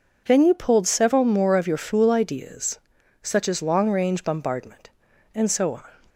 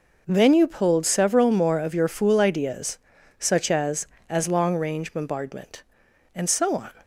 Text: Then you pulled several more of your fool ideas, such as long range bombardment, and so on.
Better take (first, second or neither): first